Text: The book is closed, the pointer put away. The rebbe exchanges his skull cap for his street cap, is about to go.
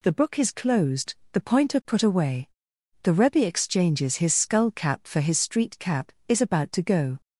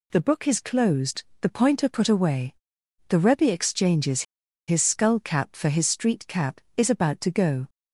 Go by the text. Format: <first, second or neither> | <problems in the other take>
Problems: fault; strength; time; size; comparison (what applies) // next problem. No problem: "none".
first | pauses between "exchanges" and "his"; at 4.2 s; 0.45 s long